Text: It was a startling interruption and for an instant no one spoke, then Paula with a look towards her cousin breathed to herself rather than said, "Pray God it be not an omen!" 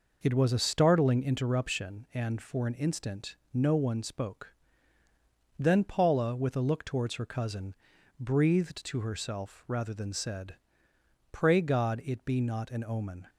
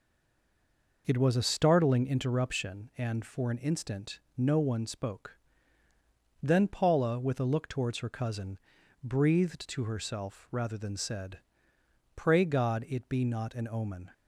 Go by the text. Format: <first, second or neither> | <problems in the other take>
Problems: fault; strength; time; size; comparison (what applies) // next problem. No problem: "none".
first | stays silent before the first word; until 1.0 s; 1.0 s long // pauses between "instant" and "no"; slight; at 4.1 s; 0.18 s long; slight in the first // pauses between "cousin" and "breathed"; noticeable; at 8.5 s; 0.46 s long; noticeable in the first